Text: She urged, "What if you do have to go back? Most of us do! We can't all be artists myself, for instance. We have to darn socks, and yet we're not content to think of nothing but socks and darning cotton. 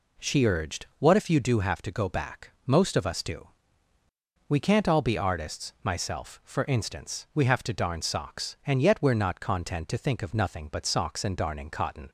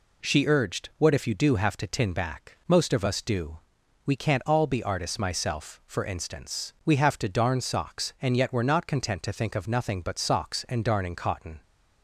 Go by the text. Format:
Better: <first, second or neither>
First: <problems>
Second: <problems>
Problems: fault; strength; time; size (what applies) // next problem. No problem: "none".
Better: first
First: none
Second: says "tin" for "go"; at 1.8 s